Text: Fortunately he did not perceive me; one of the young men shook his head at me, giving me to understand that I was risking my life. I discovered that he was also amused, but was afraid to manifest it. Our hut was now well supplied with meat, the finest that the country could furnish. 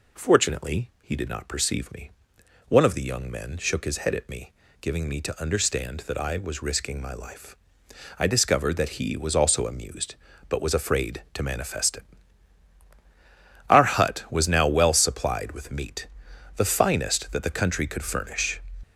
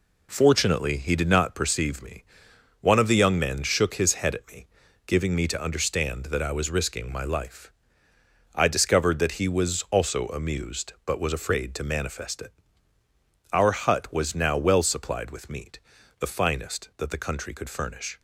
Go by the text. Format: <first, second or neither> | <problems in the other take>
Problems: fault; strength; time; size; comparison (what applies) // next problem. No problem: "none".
neither | none